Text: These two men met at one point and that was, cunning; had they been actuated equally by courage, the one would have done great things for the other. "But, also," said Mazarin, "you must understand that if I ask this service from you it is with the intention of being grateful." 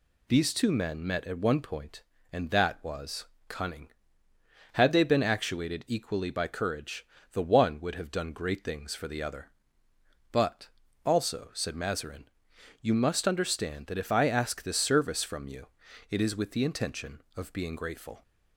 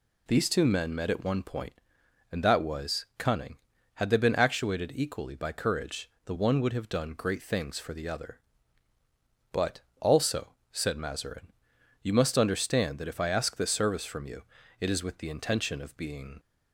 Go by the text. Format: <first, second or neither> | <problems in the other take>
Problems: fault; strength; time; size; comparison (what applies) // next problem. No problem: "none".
first | pauses between "you" and "it"; slight; at 14.4 s; 0.36 s long; also in the first // stops before "grateful"; at 16.3 s